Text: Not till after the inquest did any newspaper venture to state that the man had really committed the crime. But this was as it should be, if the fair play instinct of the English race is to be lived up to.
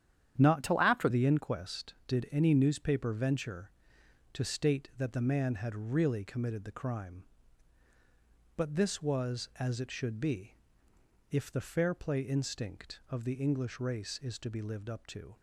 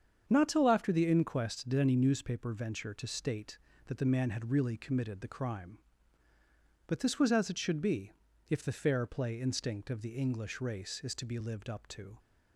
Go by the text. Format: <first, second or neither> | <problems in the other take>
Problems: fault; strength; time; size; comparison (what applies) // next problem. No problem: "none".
second | starts louder than the rest; strong; until 1.4 s; 9.5 dB; strong in the second // changes voice from "till" to "after"; from 0.6 to 1.0 s; 0.4 s long